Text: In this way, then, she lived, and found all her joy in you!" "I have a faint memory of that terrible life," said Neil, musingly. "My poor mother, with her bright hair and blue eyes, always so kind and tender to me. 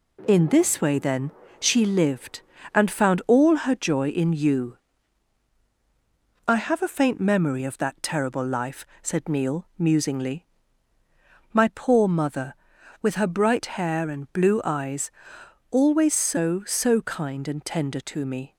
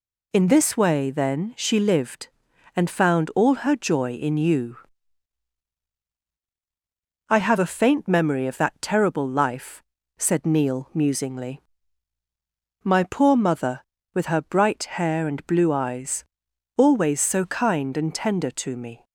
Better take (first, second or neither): second